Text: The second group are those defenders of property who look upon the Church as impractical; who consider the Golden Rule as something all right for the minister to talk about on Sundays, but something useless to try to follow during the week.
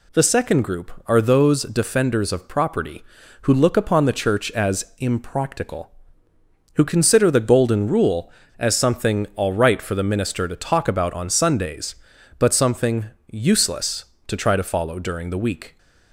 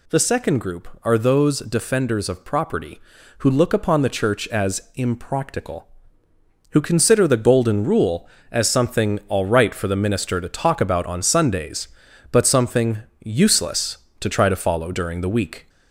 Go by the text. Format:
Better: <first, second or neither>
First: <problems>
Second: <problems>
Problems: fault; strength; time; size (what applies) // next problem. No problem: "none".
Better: first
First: pauses between "something" and "useless"; slight; at 13.0 s; 0.26 s long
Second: gets louder; slight; throughout; 2.5 dB // pauses between "something" and "useless"; slight; at 12.9 s; 0.26 s long